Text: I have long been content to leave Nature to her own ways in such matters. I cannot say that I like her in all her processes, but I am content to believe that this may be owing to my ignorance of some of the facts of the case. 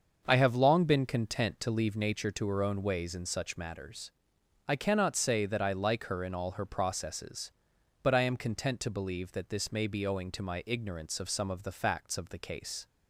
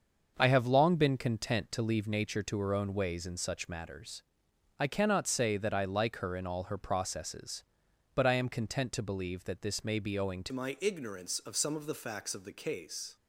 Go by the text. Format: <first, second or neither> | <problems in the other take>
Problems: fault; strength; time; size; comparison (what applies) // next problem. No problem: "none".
first | starts louder than the rest; until 1.3 s; 6.5 dB; also in the first // changes voice at "my"; from 10.5 s on; 2.6 s long